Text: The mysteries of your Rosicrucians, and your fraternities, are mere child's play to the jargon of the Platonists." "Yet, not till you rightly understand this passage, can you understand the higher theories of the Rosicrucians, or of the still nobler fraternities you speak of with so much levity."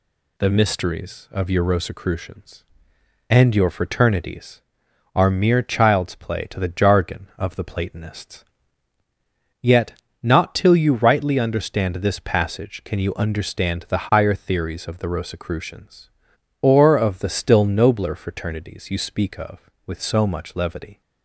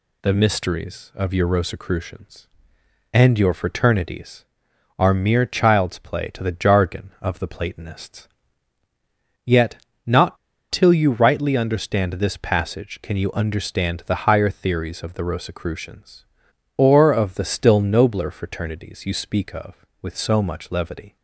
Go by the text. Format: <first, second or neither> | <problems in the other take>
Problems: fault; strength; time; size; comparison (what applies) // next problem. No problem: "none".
first | pauses between "not" and "till"; slight; at 10.3 s; 0.34 s long